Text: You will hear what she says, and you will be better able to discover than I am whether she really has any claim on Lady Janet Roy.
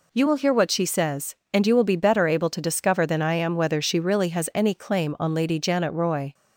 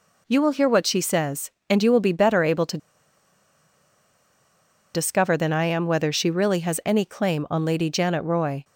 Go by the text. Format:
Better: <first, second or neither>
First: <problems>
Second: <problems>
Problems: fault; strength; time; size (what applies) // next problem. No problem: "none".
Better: first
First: none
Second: pauses between "to" and "discover"; strong; at 2.7 s; 2.1 s long